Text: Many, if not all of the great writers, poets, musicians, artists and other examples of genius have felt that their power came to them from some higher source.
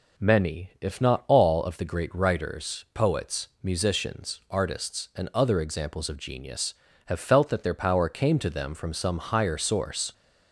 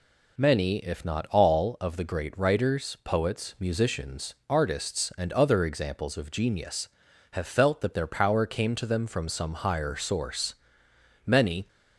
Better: first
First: none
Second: goes on to say "Many"; slight; from 11.2 s on; 0.42 s long

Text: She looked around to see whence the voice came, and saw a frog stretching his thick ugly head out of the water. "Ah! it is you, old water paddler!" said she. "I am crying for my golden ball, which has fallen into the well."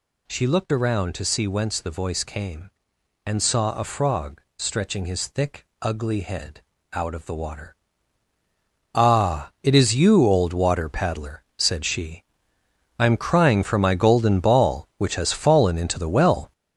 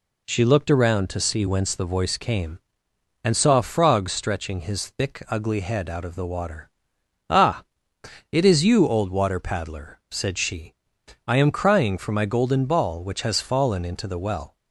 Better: second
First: gets louder; throughout; 7 dB // pauses between "frog" and "stretching"; slight; at 4.3 s; 0.16 s long // pauses between "thick" and "ugly"; slight; at 5.6 s; 0.16 s long // pauses between "head" and "out"; slight; at 6.6 s; 0.30 s long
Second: none

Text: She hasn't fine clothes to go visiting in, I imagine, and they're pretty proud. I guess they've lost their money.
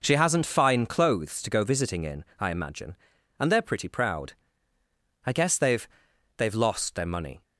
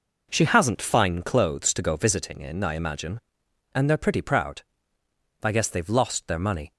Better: second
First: says "they've" twice; at 6.3 s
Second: none

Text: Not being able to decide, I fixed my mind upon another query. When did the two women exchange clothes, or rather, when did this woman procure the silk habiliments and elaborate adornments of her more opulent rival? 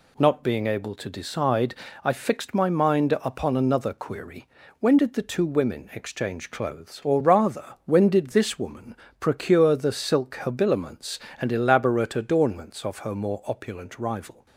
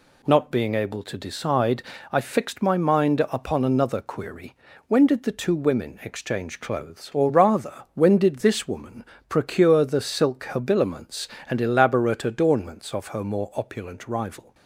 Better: neither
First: pauses between "woman" and "procure"; slight; at 8.9 s; 0.28 s long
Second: pauses between "woman" and "procure"; slight; at 9.0 s; 0.28 s long

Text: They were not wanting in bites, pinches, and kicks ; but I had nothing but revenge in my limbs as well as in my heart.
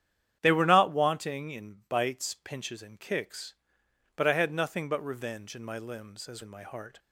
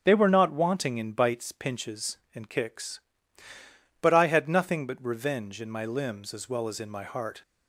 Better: second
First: starts louder than the rest; strong; until 1.4 s; 9.5 dB // skips "well as"; at 6.4 s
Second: starts louder than the rest; strong; until 1.0 s; 7.5 dB

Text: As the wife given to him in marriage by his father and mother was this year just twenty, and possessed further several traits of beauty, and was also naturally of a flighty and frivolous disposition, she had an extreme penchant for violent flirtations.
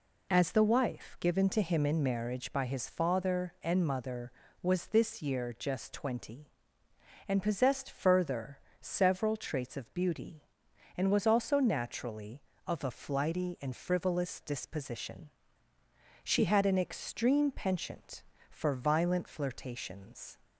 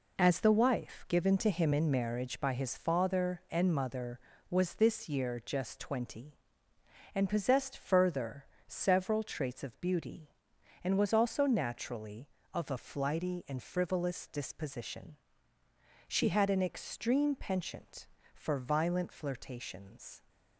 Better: first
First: pauses between "further" and "several"; slight; at 8.5 s; 0.22 s long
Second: gets quieter; strong; throughout; 8 dB // pauses between "further" and "several"; slight; at 8.4 s; 0.22 s long

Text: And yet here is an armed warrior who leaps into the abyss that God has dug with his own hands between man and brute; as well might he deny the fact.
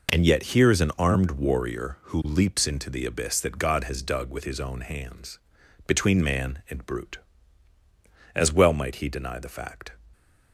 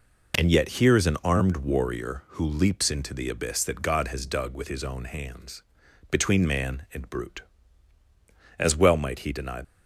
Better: first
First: pauses between "hands" and "between"; noticeable; at 5.3 s; 0.50 s long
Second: pauses between "hands" and "between"; noticeable; at 5.6 s; 0.50 s long // stops before "the fact"; at 9.6 s

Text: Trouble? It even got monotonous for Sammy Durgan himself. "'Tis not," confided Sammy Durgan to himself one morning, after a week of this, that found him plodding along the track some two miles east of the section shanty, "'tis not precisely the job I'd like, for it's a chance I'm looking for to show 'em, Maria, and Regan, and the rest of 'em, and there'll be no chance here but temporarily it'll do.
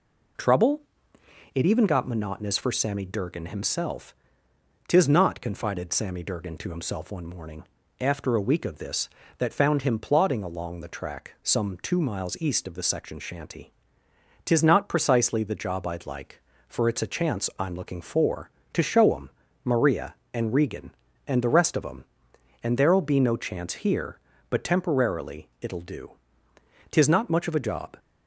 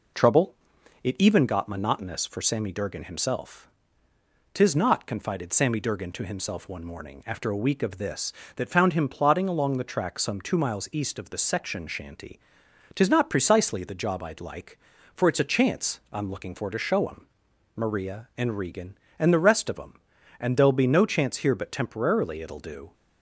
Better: second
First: goes on to say "Tis not much of a job"; noticeable; from 26.9 s on; 1.0 s long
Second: none

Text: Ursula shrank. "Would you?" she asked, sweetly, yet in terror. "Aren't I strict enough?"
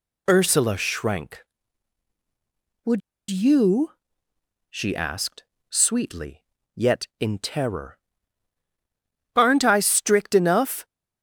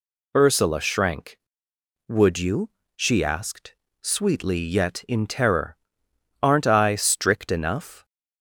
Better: second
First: pauses between "Would" and "you"; slight; at 3.0 s; 0.30 s long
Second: none

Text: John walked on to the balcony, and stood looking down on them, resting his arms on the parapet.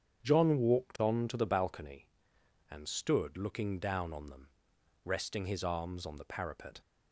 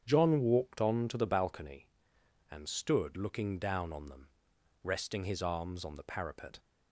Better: neither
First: starts louder than the rest; strong; until 1.2 s; 8 dB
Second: starts louder than the rest; strong; until 1.0 s; 8 dB

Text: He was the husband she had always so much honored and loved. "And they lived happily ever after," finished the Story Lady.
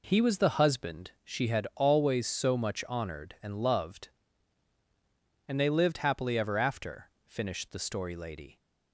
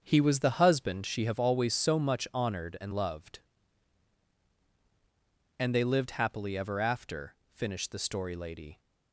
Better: first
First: none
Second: starts louder than the rest; until 1.0 s; 7 dB // says "have" for "had"; at 1.2 s

